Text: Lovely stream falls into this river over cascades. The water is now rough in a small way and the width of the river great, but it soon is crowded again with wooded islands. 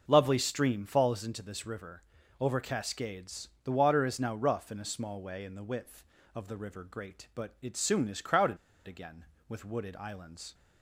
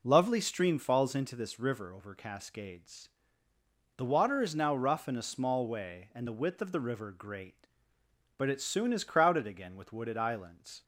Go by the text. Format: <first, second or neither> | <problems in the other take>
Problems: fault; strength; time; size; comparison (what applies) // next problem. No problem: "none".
second | starts louder than the rest; noticeable; until 1.0 s; 6 dB // pauses between "river" and "over"; at 2.0 s; 0.38 s long // pauses between "crowded" and "again"; slight; at 8.5 s; 0.30 s long